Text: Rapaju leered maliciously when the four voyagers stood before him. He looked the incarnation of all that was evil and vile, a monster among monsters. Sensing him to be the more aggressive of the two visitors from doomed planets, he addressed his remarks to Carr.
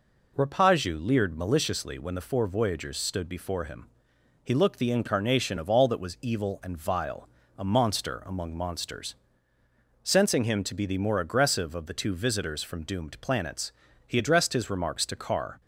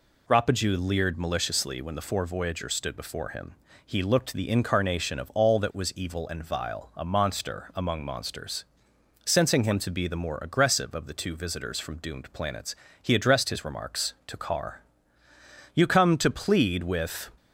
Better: first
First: none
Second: goes on to say "You come to plead with"; from 15.7 s on; 1.5 s long

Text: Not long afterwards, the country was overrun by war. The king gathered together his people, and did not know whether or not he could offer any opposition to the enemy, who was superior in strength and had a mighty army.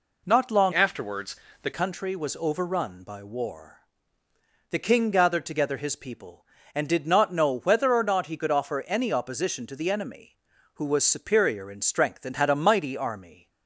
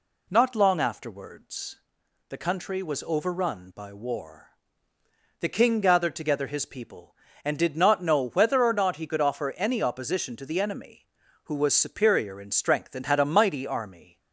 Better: second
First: changes voice from "afterwards" to "the"; from 0.7 to 1.7 s; 1.0 s long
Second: none

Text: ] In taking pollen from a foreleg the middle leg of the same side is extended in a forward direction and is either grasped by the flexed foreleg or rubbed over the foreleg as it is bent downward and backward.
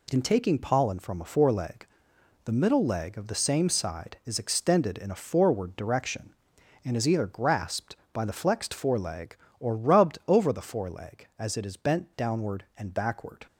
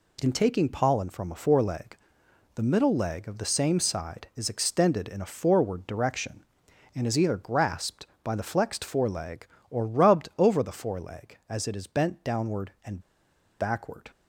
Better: first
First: pauses between "foreleg" and "the"; noticeable; at 1.8 s; 0.60 s long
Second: pauses between "foreleg" and "the"; noticeable; at 1.9 s; 0.60 s long // pauses between "and" and "backward"; noticeable; at 12.9 s; 0.60 s long

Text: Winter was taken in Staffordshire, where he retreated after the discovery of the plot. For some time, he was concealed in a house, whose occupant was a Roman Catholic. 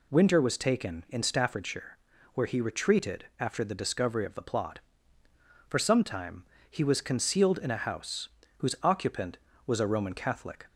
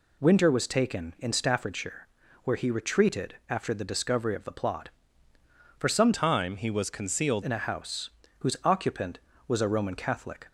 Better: first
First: none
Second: changes voice from "time" to "concealed"; from 6.1 to 7.4 s; 1.3 s long

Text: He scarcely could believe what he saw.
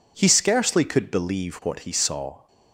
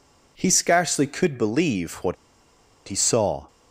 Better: first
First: none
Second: pauses between "what" and "he"; noticeable; at 2.1 s; 0.73 s long

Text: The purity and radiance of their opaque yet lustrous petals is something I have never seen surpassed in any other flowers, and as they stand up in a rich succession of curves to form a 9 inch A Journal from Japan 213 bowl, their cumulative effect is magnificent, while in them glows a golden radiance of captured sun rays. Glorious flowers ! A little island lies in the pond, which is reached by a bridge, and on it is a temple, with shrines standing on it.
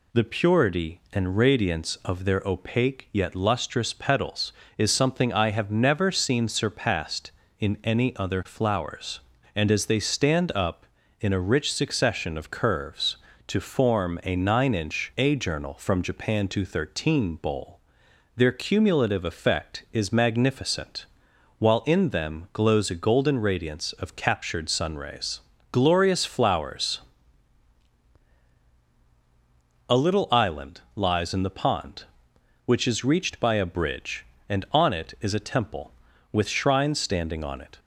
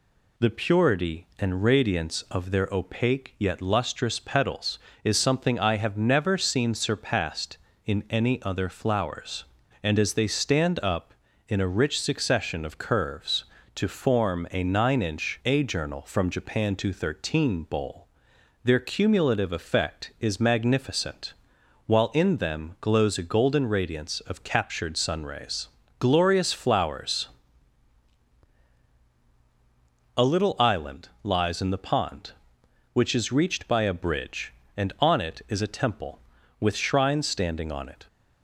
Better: neither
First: pauses between "island" and "lies"; slight; at 30.7 s; 0.16 s long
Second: pauses between "island" and "lies"; slight; at 31.0 s; 0.16 s long

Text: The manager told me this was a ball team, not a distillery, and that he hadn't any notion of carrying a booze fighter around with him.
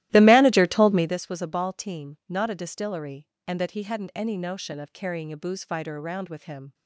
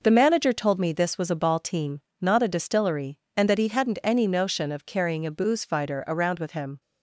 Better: second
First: starts louder than the rest; strong; until 1.2 s; 15 dB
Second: none

